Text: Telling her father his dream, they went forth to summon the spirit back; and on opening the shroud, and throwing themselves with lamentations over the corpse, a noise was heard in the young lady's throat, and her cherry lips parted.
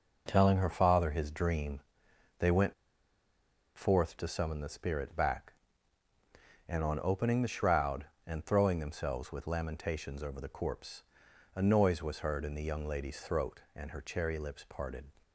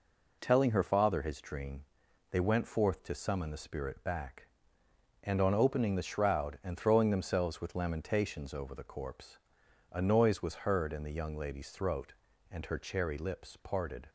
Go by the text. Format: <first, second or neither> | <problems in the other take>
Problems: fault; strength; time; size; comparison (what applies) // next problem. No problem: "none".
second | pauses between "went" and "forth"; at 2.7 s; 1.0 s long